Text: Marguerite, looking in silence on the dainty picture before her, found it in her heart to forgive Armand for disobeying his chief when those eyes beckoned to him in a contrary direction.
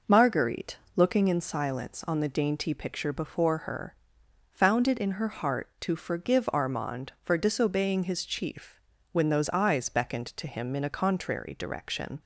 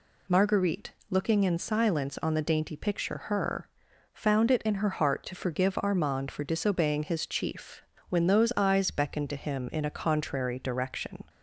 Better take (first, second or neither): first